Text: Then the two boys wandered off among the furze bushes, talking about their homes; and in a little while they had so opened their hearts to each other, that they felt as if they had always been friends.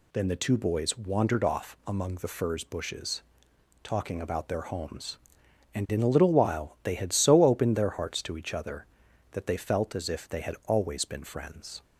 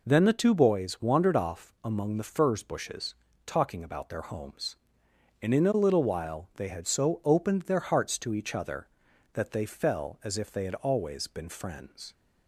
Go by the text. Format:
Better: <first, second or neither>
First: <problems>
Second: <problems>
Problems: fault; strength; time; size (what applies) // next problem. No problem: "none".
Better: first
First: none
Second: says "fell" for "felt"; at 9.6 s